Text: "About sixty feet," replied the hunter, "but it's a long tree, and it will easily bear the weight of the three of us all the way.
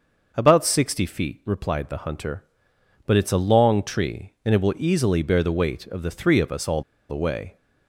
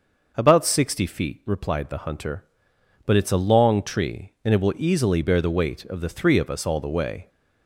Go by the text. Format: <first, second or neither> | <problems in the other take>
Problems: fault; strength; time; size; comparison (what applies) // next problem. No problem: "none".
second | starts louder than the rest; until 1.3 s; 6 dB; noticeable in the second // pauses between "all" and "the"; slight; at 6.8 s; 0.26 s long